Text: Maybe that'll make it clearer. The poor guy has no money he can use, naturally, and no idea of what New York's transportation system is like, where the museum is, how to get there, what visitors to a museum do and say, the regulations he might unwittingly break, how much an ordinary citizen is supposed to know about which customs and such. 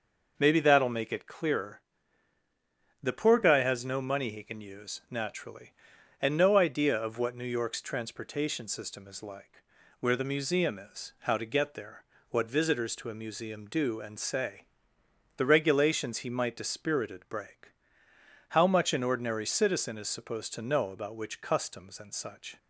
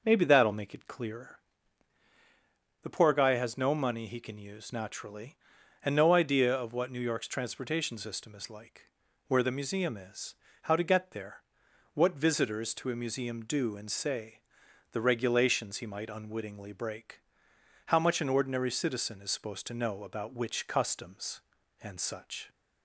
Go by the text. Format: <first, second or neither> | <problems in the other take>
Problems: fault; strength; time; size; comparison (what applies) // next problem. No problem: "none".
second | says "dispirited" for "unwittingly"; at 16.5 s